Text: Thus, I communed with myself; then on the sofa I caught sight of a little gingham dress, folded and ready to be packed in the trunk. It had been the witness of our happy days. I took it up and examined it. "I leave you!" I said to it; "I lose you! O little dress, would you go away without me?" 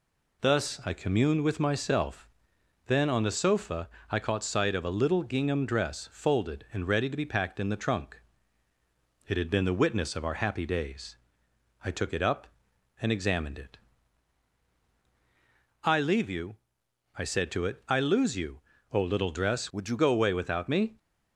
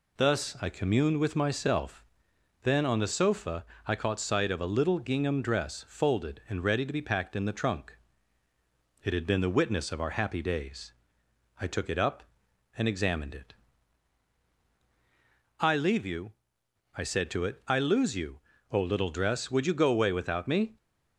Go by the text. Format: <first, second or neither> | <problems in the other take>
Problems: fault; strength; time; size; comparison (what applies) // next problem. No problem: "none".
second | pauses between "sofa" and "I"; slight; at 3.8 s; 0.22 s long; slight in the second // changes voice from "would" to "you"; from 19.7 to 19.9 s; 0.2 s long